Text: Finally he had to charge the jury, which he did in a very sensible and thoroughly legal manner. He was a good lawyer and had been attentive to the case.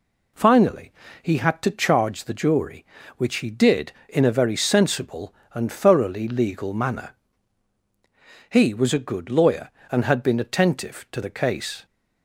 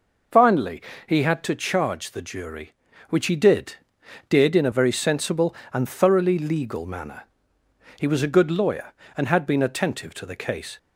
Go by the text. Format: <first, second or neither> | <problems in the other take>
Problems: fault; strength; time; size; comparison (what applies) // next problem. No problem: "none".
first | pauses between "Finally" and "he"; slight; at 0.8 s; 0.24 s long; slight in the first // says "did" twice; at 4.2 s